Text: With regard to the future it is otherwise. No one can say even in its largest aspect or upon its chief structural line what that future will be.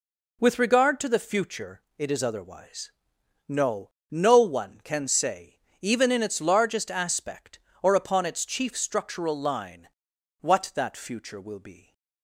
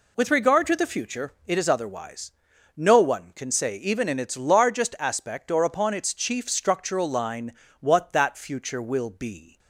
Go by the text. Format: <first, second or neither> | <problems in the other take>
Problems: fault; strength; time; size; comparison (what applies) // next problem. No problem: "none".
second | pauses between "future" and "it"; slight; at 1.8 s; 0.16 s long // says "No" twice; at 4.1 s // pauses between "say" and "even"; slight; at 5.5 s; 0.22 s long // pauses between "line" and "what"; noticeable; at 9.8 s; 0.52 s long; slight in the second